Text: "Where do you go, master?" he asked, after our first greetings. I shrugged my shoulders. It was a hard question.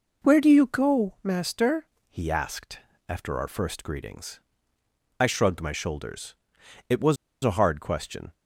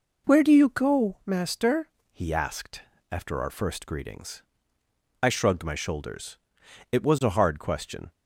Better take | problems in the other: second | pauses between "was" and "a"; slight; at 7.1 s; 0.28 s long

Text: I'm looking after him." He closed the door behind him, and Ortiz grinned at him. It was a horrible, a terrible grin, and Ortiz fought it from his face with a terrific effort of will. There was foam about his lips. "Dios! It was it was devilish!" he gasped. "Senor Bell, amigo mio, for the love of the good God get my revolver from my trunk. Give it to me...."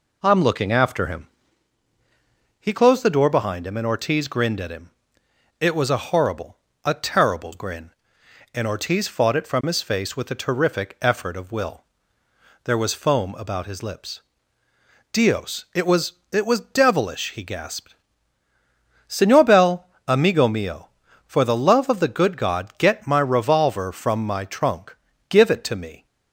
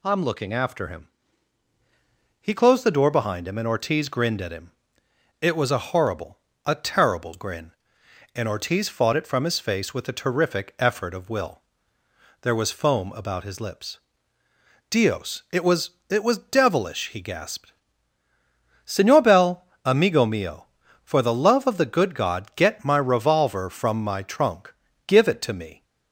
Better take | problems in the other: second | starts louder than the rest; slight; until 1.5 s; 3.5 dB // pauses between "was" and "it"; slight; at 16.1 s; 0.18 s long; slight in the second

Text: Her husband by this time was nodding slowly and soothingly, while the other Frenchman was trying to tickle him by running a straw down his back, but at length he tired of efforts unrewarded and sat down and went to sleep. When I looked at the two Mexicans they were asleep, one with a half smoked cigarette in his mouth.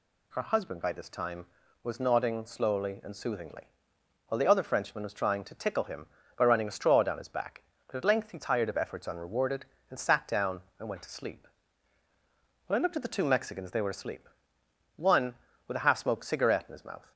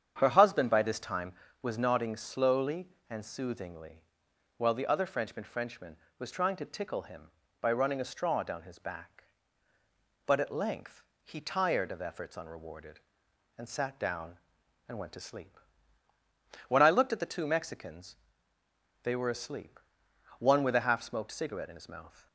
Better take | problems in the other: first | starts louder than the rest; strong; until 1.1 s; 8.5 dB // says "Frenchman" twice; at 5.4 s // pauses between "length" and "he"; slight; at 11.0 s; 0.20 s long // pauses between "Mexicans" and "they"; noticeable; at 18.1 s; 0.86 s long

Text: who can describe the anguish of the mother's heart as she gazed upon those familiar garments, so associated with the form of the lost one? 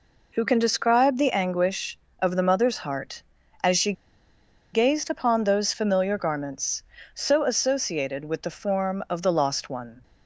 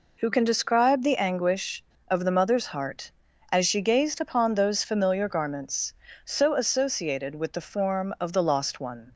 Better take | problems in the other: second | pauses between "she" and "gazed"; noticeable; at 3.9 s; 0.80 s long

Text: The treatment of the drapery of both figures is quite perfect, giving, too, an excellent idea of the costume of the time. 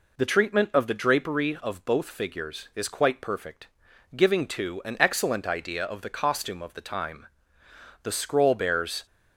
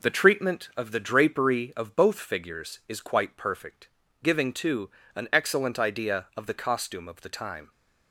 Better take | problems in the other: second | goes on to say "The scroll bears"; noticeable; from 8.0 s on; 1.0 s long

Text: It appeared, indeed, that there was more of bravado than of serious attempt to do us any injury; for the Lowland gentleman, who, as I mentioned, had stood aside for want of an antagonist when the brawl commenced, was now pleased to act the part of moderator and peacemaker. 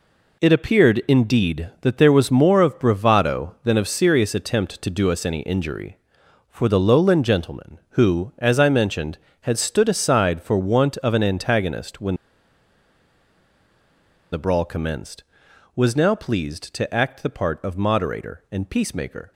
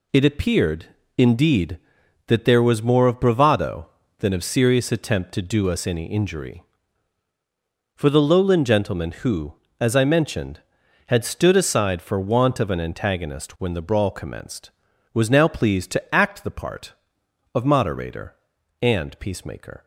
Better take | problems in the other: second | pauses between "when" and "the"; strong; at 12.1 s; 2.1 s long

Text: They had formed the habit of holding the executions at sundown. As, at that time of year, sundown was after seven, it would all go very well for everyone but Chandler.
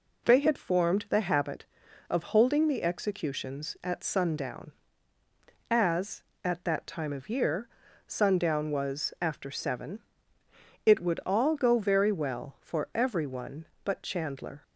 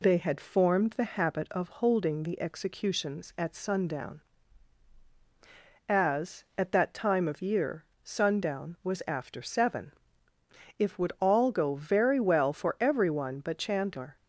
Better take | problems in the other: first | says "if" for "it"; at 10.7 s

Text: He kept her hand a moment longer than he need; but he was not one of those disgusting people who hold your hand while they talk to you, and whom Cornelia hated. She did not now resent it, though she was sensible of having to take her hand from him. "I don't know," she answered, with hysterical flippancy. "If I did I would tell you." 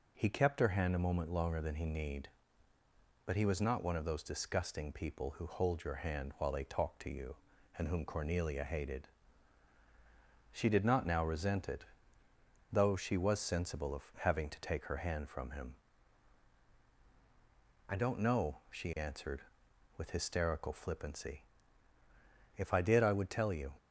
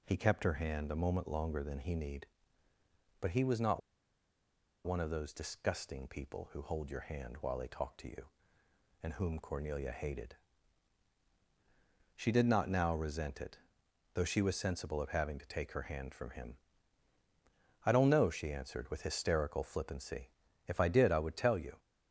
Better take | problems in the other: first | pauses between "not" and "one"; at 3.8 s; 1.0 s long

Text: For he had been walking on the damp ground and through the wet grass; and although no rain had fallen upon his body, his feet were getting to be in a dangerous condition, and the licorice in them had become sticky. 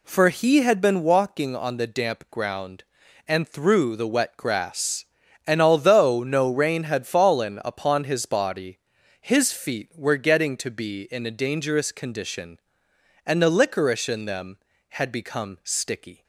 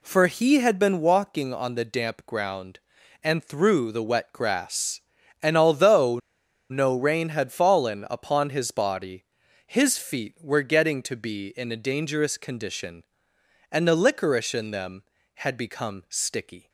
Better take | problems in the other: first | pauses between "although" and "no"; noticeable; at 6.1 s; 0.51 s long

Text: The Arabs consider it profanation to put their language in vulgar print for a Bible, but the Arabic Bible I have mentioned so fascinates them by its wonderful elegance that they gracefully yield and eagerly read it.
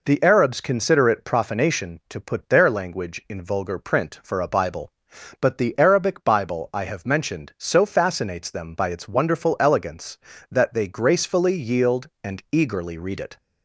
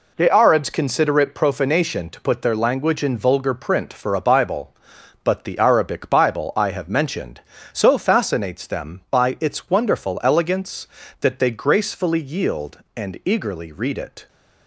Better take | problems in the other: neither | none

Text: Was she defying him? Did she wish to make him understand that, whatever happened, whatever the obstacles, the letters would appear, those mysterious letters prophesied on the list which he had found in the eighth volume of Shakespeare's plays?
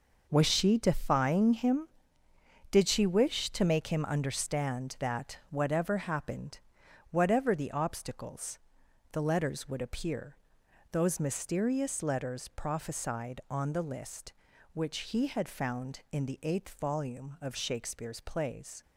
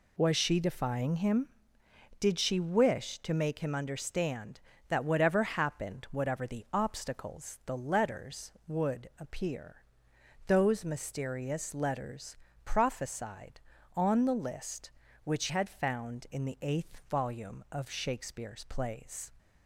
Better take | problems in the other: first | pauses between "letters" and "prophesied"; slight; at 12.3 s; 0.30 s long // skips "he"; at 15.4 s

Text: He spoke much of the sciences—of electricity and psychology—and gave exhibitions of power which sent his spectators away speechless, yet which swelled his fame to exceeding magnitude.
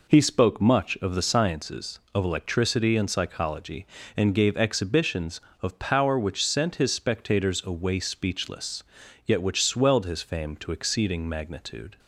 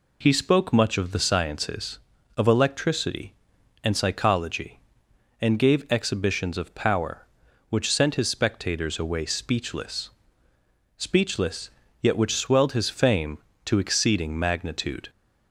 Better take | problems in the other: first | says "speechless" twice; at 10.9 s

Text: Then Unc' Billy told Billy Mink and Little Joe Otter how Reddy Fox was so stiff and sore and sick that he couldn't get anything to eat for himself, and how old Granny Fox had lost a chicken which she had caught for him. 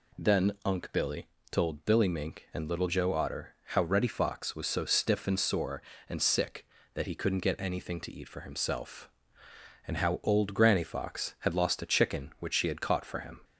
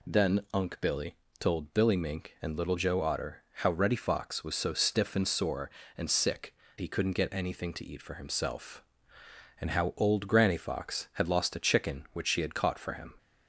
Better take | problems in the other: first | pauses between "Billy" and "told"; slight; at 1.1 s; 0.24 s long; slight in the first // pauses between "Otter" and "how"; slight; at 3.3 s; 0.16 s long; slight in the first // skips "that"; at 6.6 s

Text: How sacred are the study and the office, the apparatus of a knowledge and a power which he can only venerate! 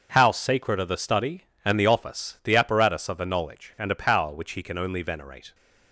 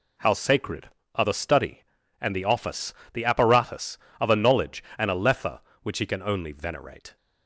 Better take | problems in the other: first | says "lethe" for "power"; at 5.1 s

